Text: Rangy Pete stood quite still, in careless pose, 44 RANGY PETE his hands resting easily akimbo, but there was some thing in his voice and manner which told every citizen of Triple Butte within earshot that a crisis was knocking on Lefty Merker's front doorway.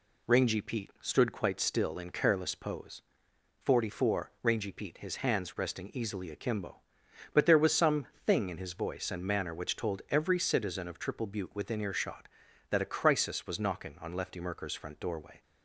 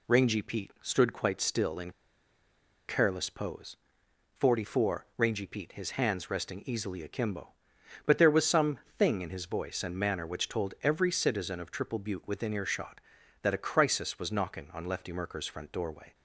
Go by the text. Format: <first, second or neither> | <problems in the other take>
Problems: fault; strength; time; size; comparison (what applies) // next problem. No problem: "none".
first | pauses between "in" and "careless"; noticeable; at 1.9 s; 0.96 s long // pauses between "some" and "thing"; slight; at 8.7 s; 0.18 s long; slight in the first